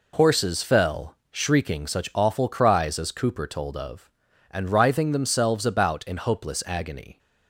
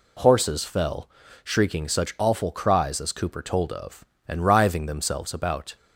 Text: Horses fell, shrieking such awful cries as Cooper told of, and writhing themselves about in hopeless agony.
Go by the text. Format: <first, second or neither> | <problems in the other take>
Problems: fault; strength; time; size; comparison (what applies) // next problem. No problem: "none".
first | stops before "in hopeless agony"; at 5.7 s